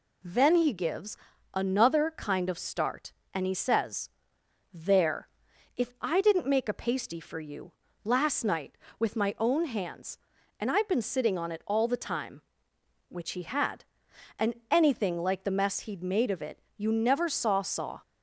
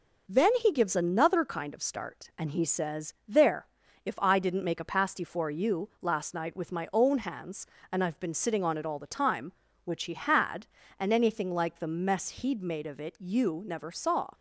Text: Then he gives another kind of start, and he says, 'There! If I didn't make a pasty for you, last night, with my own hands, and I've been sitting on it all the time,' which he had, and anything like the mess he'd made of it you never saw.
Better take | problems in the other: second | pauses between "gives" and "another"; at 1.1 s; 0.38 s long // pauses between "and" and "anything"; slight; at 14.5 s; 0.16 s long // pauses between "it" and "you"; slight; at 16.6 s; 0.16 s long // says "saw" twice; at 17.6 s

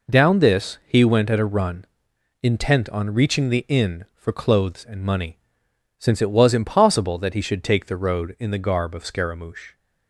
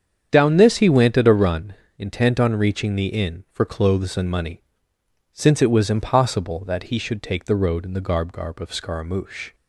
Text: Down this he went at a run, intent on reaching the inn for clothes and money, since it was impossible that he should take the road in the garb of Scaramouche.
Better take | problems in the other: first | starts louder than the rest; strong; until 1.3 s; 8 dB // says "garb" twice; at 8.3 s

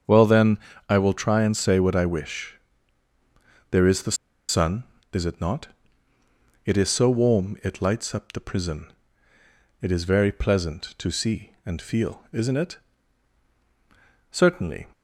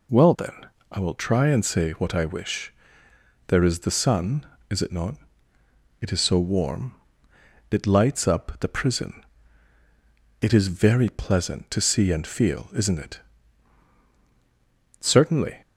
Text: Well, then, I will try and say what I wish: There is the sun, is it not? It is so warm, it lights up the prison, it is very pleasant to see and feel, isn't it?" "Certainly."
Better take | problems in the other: second | starts louder than the rest; strong; until 1.3 s; 7.5 dB // pauses between "the" and "sun"; slight; at 4.1 s; 0.34 s long

